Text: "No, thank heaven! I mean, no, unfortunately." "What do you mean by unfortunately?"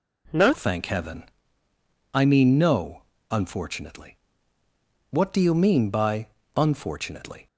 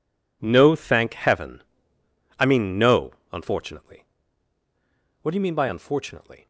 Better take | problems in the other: second | changes voice at "thank"; from 0.5 s on; 6.9 s long // pauses between "by" and "unfortunately"; slight; at 6.2 s; 0.30 s long

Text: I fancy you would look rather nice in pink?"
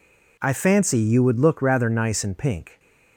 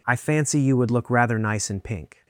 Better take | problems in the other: neither | none

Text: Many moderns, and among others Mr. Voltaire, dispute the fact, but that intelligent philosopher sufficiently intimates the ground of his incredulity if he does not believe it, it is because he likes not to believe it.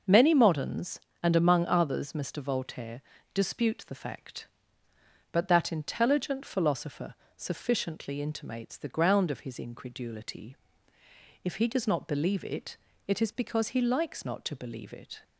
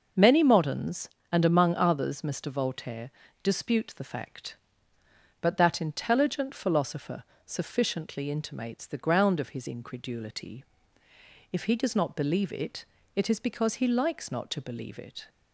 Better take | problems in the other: neither | starts louder than the rest; noticeable; the same in both // pauses between "philosopher" and "sufficiently"; slight; the same in both // pauses between "incredulity" and "if"; noticeable; the same in both

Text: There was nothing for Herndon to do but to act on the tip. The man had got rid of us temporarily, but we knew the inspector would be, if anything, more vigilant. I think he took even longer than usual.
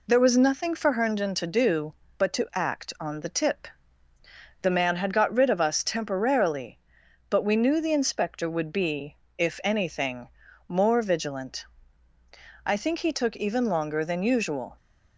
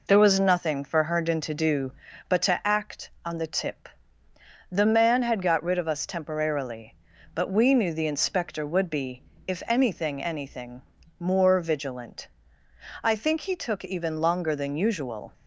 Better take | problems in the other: first | says "anything" twice; at 10.2 s

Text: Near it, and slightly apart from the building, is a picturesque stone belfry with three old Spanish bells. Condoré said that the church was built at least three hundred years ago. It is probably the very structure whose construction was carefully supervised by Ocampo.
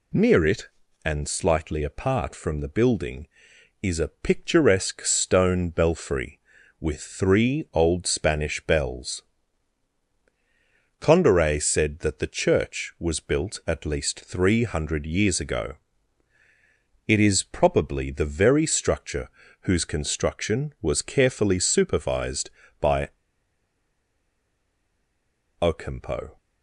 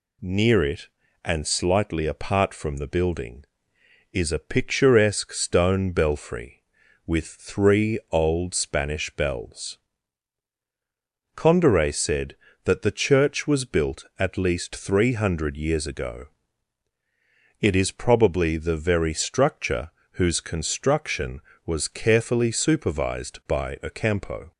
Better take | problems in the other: second | pauses between "structure" and "whose"; slight; at 19.2 s; 0.32 s long; slight in the second // pauses between "by" and "Ocampo"; strong; at 23.0 s; 2.5 s long

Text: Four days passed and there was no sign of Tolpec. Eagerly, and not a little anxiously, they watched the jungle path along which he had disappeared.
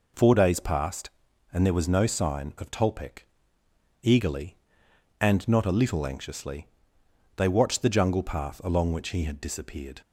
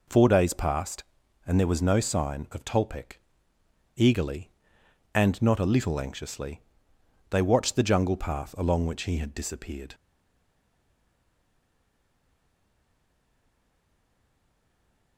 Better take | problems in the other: first | stays silent after the last word; strong; from 9.9 s on; 5.2 s long

